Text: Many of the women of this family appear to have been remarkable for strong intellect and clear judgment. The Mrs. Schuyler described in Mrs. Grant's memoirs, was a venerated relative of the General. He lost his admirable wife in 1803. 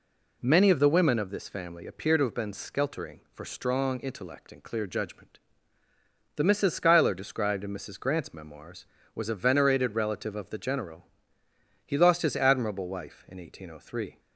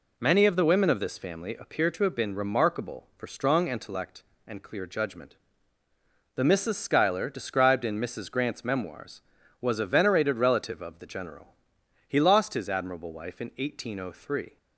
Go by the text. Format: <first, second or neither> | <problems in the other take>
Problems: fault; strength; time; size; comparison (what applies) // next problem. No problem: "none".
second | says "skeltering" for "remarkable"; at 2.5 s